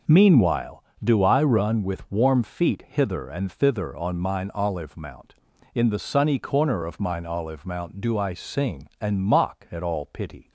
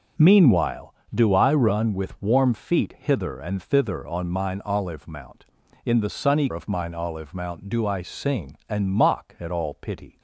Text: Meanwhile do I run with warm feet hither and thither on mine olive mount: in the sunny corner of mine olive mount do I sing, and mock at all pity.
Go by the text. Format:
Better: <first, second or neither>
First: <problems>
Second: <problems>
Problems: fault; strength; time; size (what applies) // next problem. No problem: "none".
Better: first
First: none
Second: skips "corner"; at 6.5 s